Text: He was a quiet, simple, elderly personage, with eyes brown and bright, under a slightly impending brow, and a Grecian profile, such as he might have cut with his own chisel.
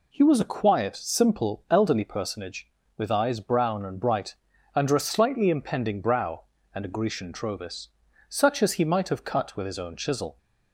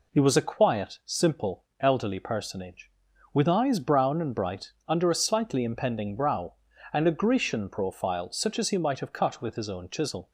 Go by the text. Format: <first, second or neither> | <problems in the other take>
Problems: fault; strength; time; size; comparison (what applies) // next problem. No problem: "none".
second | says "trovis" for "profile"; at 7.3 s